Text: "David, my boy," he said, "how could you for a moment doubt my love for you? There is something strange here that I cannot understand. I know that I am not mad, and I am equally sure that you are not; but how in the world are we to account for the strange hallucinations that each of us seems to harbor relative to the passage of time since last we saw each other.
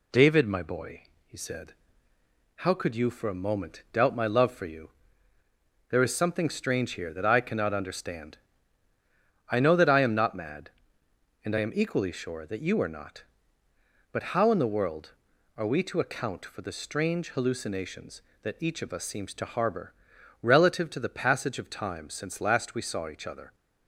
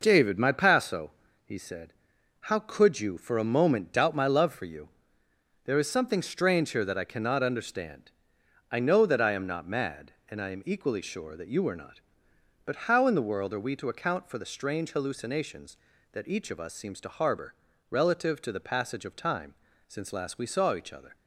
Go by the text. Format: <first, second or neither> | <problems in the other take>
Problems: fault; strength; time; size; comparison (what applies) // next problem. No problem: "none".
first | says "paso" for "boy"; at 0.5 s // pauses between "harbor" and "relative"; at 17.5 s; 0.38 s long; noticeable in the first // pauses between "time" and "since"; slight; at 19.5 s; 0.34 s long